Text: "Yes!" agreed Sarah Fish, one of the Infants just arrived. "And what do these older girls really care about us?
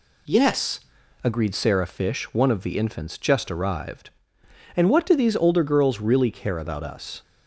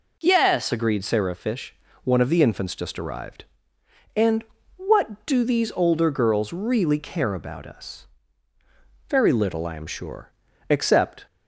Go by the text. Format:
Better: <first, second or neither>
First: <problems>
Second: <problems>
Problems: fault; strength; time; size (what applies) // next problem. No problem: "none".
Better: first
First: none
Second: pauses between "And" and "what"; slight; at 4.4 s; 0.34 s long // goes on to say "Very little I am sure except"; strong; from 9.0 s on; 2.1 s long